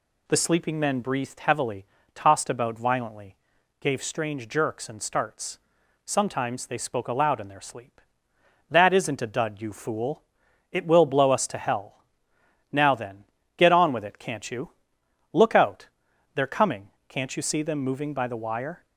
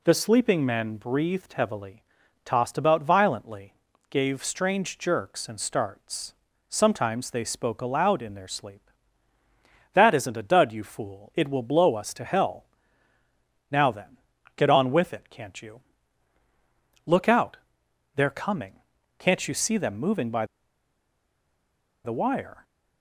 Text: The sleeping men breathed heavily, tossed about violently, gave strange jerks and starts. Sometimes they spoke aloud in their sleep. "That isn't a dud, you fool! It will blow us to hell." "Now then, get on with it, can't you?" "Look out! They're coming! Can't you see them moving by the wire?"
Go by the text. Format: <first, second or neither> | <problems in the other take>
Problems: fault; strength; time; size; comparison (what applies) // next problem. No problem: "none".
first | pauses between "by" and "the"; strong; at 20.4 s; 1.5 s long